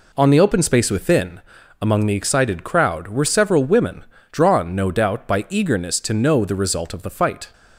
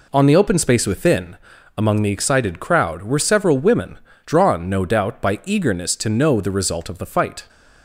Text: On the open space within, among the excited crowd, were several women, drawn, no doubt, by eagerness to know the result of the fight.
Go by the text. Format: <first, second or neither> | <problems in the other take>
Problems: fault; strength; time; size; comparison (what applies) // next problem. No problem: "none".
neither | none